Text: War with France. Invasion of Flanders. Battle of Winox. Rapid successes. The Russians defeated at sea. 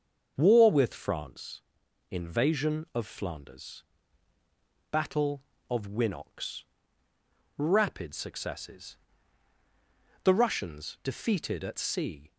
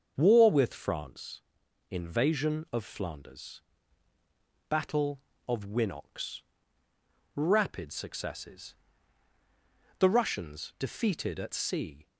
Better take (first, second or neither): neither